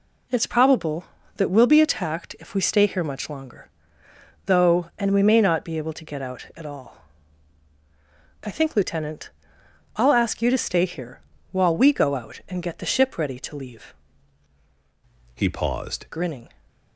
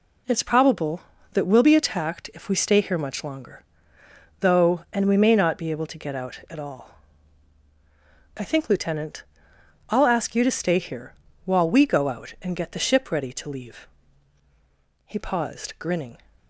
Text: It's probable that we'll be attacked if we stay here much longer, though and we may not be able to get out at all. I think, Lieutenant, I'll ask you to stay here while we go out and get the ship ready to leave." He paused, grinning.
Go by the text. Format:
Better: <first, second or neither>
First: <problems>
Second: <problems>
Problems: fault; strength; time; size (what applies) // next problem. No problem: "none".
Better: second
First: pauses between "here" and "while"; slight; at 11.2 s; 0.28 s long // changes voice from "He" to "paused"; from 15.3 to 16.0 s; 0.7 s long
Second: pauses between "here" and "while"; slight; at 11.1 s; 0.28 s long